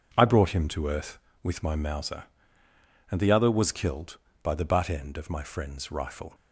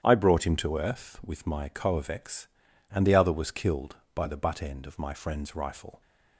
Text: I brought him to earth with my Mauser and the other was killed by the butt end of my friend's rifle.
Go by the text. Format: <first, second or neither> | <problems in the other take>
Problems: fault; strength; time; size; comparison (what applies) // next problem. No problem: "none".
first | starts louder than the rest; strong; until 1.0 s; 9.5 dB // says "Coavex" for "Mauser"; at 1.6 s